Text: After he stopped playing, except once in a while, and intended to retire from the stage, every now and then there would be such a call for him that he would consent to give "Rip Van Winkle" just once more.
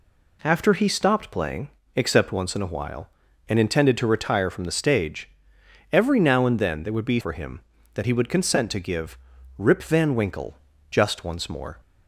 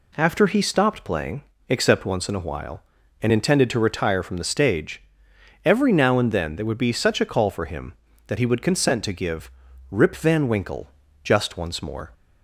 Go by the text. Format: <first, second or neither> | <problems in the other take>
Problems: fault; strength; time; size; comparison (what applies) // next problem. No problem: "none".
second | skips "such a call"; at 7.1 s // pauses between "give" and "Rip"; at 9.1 s; 0.40 s long; also in the second // pauses between "Winkle" and "just"; slight; at 10.5 s; 0.32 s long; slight in the second